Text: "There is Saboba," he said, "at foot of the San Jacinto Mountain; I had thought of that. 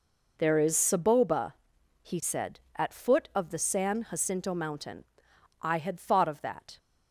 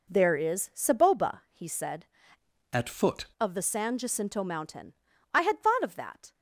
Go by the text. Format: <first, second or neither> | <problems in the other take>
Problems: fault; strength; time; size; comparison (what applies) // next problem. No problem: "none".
first | changes voice from "at" to "foot"; from 2.7 to 3.2 s; 0.5 s long